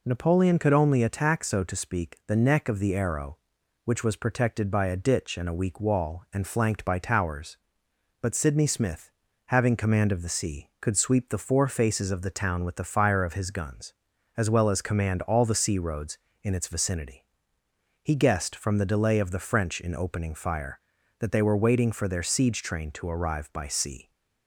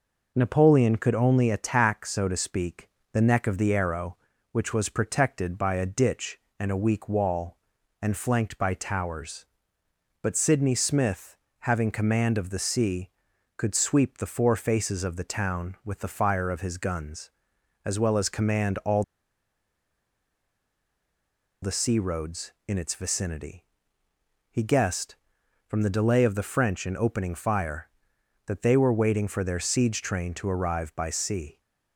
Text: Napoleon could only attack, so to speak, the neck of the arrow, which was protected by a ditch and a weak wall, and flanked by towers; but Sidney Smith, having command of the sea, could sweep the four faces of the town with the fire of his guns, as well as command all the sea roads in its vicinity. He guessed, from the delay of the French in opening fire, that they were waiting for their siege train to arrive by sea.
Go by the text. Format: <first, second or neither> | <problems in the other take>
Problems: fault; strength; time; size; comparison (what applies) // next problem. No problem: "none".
first | pauses between "all" and "the"; strong; at 19.0 s; 2.6 s long